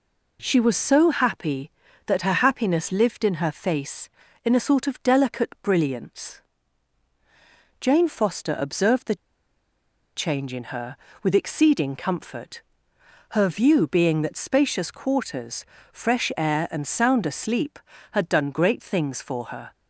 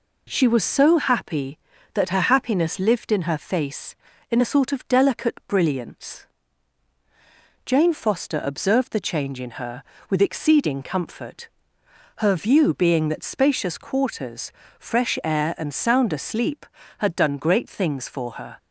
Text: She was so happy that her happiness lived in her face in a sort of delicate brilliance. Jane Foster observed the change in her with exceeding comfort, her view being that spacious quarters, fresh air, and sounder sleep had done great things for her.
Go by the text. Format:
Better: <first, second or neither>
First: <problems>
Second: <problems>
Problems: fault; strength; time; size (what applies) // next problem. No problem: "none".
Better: second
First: pauses between "the" and "change"; at 9.1 s; 1.0 s long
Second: none